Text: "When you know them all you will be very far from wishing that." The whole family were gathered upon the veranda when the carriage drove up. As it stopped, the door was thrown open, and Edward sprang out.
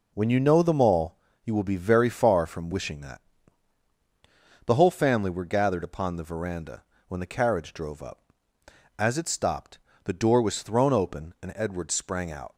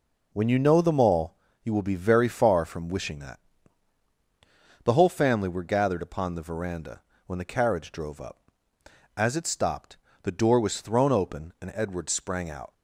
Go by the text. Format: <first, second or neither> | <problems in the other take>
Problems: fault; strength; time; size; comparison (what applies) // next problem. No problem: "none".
neither | pauses between "all" and "you"; slight; the same in both // pauses between "veranda" and "when"; slight; the same in both